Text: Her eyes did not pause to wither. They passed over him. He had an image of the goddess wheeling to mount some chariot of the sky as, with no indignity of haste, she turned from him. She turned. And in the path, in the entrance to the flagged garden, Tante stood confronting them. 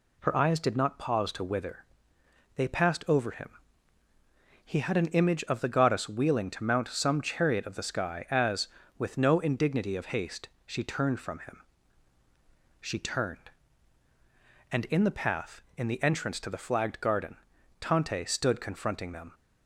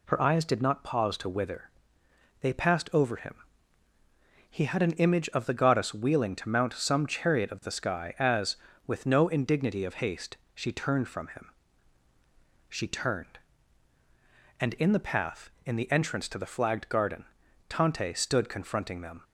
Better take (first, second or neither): neither